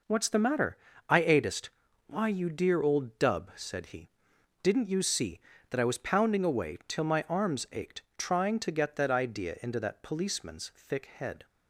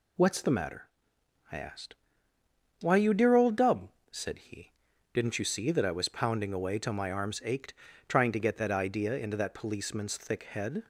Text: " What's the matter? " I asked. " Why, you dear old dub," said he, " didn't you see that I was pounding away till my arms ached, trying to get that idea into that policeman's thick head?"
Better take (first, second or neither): second